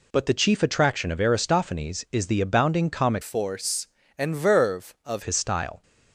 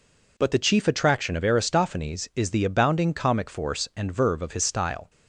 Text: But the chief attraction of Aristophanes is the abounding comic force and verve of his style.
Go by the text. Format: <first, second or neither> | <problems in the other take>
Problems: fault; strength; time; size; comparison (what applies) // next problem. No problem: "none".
second | changes voice from "force" to "of"; from 3.2 to 5.2 s; 2.0 s long